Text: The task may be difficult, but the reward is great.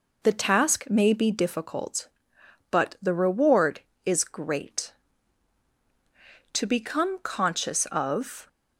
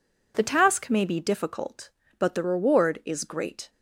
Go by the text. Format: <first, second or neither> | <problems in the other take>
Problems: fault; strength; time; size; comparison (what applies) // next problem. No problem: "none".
second | goes on to say "To become conscious of"; strong; from 6.5 s on; 1.9 s long